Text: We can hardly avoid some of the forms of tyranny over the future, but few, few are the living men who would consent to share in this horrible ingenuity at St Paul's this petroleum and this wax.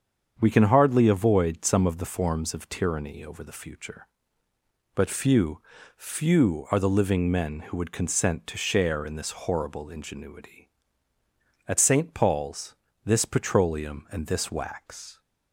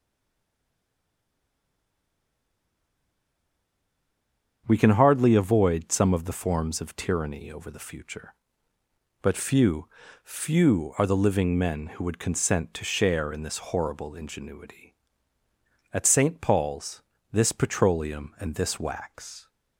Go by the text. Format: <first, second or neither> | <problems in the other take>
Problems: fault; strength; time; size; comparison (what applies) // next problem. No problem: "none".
first | stays silent before the first word; strong; until 4.6 s; 4.6 s long // starts louder than the rest; strong; until 5.6 s; 7.5 dB; strong in the first // pauses between "Paul's" and "this"; slight; at 17.0 s; 0.32 s long; slight in the first